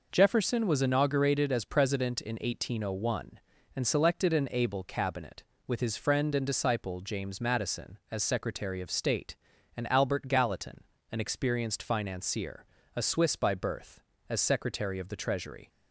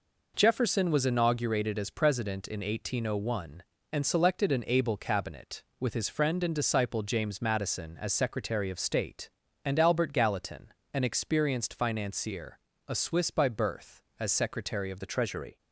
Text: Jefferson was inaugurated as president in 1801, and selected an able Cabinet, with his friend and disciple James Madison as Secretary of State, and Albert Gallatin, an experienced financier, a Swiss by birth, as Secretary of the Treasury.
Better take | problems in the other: first | changes voice at "the"; from 14.9 s on; 0.6 s long

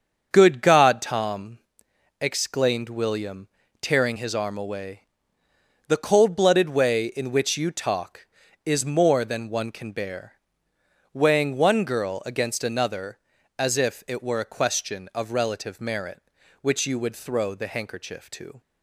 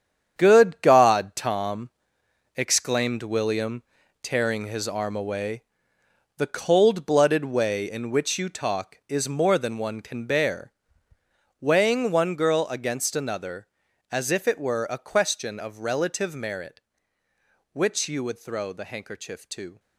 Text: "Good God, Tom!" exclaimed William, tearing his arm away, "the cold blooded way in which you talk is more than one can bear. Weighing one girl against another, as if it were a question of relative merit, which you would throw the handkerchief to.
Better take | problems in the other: first | gets quieter; strong; throughout; 10 dB // starts louder than the rest; strong; until 1.3 s; 8.5 dB; strong in the first

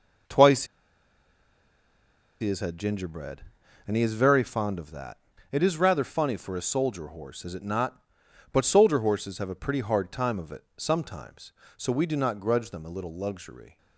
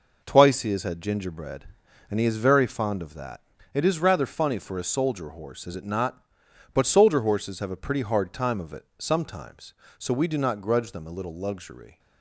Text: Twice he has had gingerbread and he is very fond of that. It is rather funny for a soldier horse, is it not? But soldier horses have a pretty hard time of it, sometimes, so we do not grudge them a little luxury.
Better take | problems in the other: second | pauses between "Twice" and "he"; strong; at 0.6 s; 1.7 s long

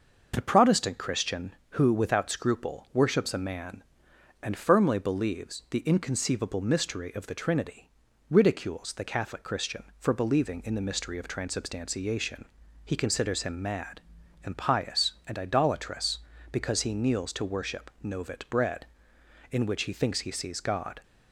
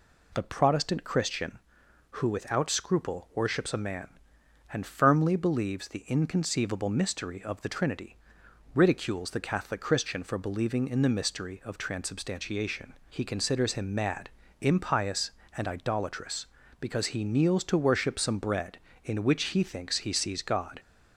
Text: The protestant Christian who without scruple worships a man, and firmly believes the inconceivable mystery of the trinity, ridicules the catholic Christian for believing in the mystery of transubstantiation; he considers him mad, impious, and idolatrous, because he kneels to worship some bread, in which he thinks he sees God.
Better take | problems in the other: second | says "novit" for "some"; at 18.0 s

